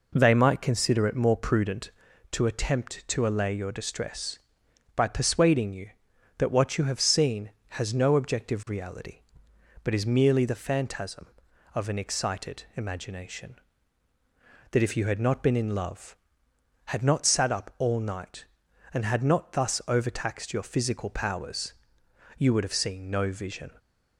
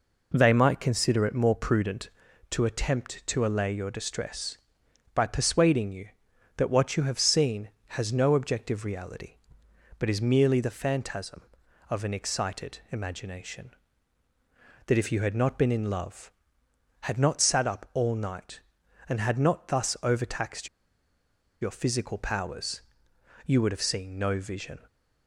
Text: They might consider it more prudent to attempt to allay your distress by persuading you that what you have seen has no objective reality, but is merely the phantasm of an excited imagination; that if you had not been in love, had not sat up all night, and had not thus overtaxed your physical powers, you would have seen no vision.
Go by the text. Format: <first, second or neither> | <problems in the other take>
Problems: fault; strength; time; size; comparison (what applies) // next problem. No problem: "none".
first | pauses between "overtaxed" and "your"; noticeable; at 20.6 s; 0.94 s long